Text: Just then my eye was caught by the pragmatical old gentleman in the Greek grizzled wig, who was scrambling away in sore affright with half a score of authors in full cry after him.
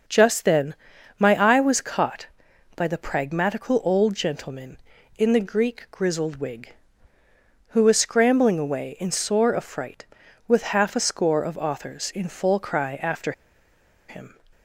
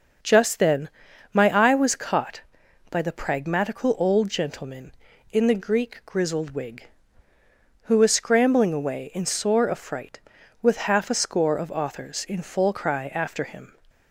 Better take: second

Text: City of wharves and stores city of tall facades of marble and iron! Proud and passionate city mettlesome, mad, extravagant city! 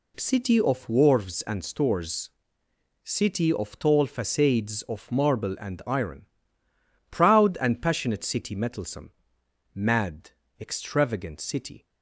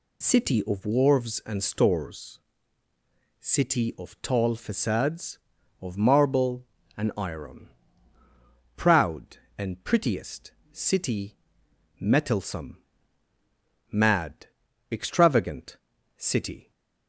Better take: first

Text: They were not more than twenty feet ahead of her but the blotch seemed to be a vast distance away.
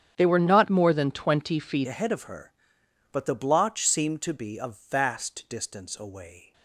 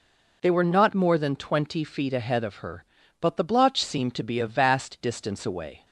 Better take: second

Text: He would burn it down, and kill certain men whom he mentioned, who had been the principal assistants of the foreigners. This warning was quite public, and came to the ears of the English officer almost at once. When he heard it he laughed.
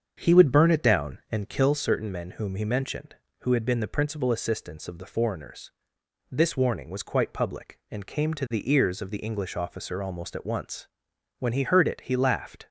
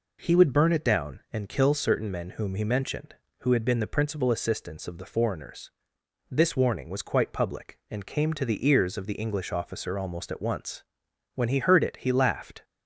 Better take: second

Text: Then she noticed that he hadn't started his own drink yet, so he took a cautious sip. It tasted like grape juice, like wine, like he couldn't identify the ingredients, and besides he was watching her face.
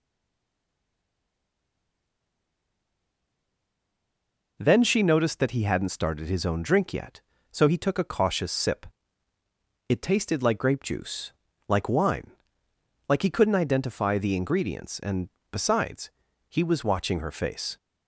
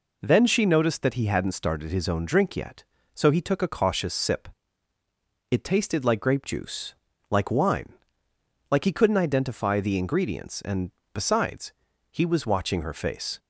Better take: second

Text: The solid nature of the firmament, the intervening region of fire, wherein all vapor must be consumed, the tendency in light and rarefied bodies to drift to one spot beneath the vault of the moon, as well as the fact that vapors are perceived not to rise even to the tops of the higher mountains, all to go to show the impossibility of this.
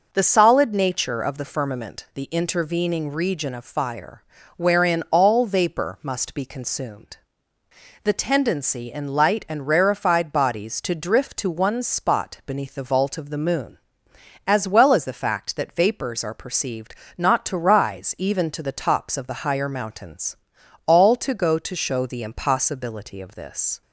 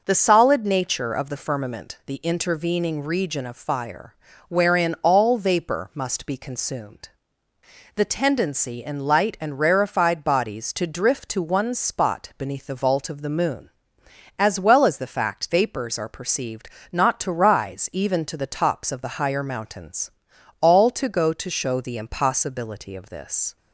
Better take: first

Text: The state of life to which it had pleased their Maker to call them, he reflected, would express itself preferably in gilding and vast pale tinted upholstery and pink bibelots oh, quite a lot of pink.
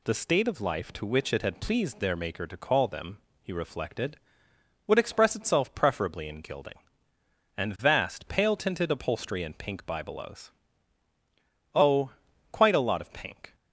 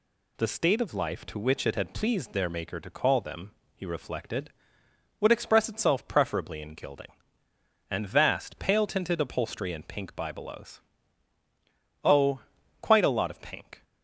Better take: neither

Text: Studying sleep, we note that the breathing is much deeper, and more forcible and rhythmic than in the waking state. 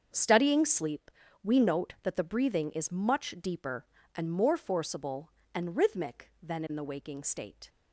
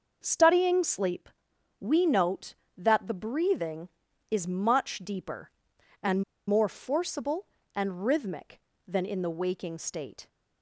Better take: first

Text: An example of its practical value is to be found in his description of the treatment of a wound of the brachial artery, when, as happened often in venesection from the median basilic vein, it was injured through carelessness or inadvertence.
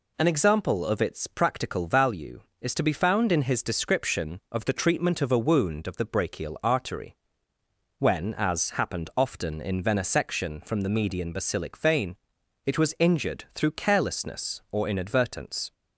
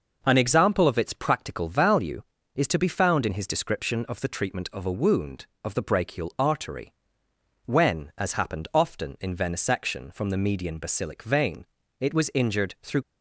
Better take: first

